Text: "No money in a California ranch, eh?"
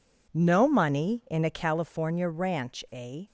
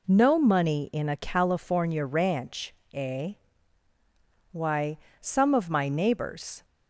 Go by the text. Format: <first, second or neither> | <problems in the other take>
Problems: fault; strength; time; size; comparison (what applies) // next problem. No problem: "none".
first | goes on to say "Why some of my neighbors"; strong; from 4.5 s on; 2.1 s long